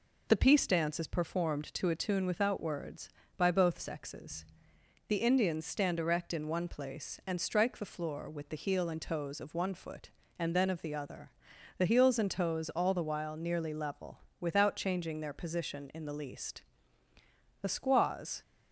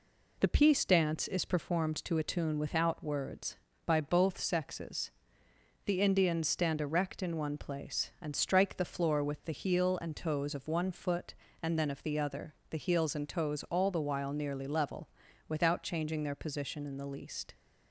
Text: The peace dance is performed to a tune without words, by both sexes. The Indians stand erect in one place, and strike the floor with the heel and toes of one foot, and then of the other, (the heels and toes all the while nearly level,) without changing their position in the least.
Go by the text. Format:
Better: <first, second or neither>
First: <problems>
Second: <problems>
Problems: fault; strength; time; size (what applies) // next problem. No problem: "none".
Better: second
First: goes on to say "The squaws"; noticeable; from 17.6 s on; 0.80 s long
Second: none